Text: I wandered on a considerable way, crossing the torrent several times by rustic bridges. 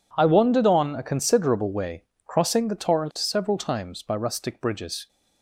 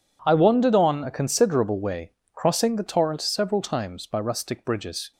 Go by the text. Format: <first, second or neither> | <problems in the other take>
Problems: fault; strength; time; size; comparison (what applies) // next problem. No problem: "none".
neither | none